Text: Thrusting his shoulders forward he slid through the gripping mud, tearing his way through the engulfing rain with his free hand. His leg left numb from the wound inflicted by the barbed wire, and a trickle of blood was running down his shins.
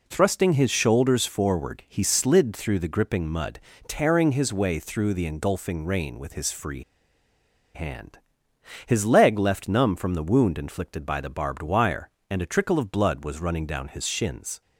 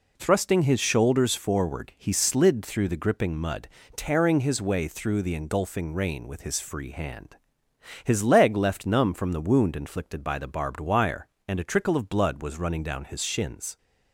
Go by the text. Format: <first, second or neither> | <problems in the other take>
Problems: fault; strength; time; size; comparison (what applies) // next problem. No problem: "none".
second | pauses between "free" and "hand"; noticeable; at 6.8 s; 0.92 s long